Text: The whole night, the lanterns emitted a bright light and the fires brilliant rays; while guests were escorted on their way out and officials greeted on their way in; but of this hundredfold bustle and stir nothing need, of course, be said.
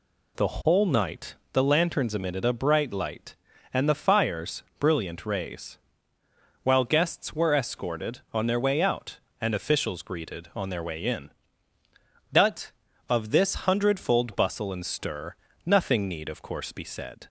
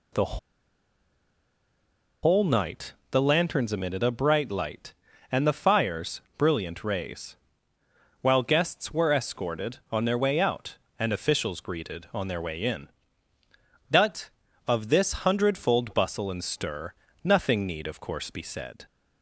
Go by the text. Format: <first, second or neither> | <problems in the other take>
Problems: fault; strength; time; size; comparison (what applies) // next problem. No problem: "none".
first | pauses between "The" and "whole"; strong; at 0.3 s; 1.8 s long // pauses between "fires" and "brilliant"; slight; at 6.2 s; 0.16 s long; slight in the first // pauses between "stir" and "nothing"; slight; at 16.9 s; 0.30 s long; slight in the first